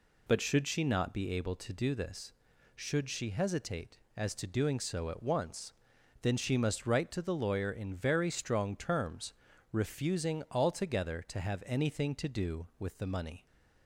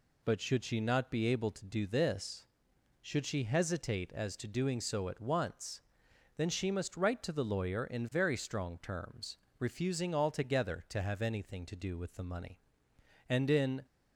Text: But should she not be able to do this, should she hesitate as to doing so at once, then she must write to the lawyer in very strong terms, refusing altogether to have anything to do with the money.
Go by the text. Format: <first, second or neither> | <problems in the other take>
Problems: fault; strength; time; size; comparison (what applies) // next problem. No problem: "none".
first | goes on to say "And in"; from 13.2 s on; 0.56 s long